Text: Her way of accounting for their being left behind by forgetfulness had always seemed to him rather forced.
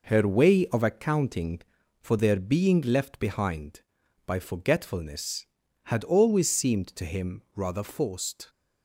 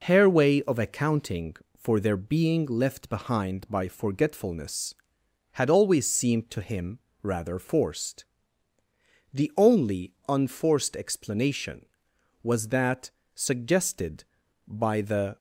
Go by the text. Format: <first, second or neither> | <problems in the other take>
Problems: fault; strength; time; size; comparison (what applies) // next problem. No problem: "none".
first | pauses between "him" and "rather"; slight; at 6.9 s; 0.24 s long // goes on to say "The only unforced explanation was that suggested by the"; strong; from 9.3 s on; 6.0 s long